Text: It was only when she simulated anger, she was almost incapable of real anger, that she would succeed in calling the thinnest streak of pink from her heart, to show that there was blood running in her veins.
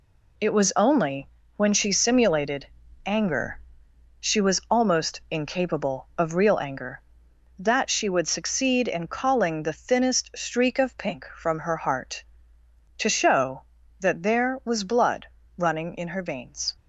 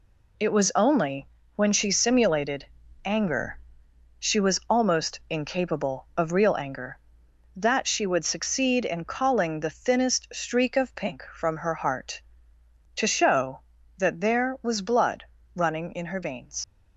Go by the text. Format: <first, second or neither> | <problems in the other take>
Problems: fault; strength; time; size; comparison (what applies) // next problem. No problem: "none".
first | pauses between "only" and "when"; slight; at 1.2 s; 0.26 s long; slight in the first // pauses between "simulated" and "anger"; at 2.6 s; 0.40 s long; also in the first // pauses between "blood" and "running"; slight; at 15.2 s; 0.32 s long; slight in the first // leaves "veins" unfinished; at 16.6 s; 75 ms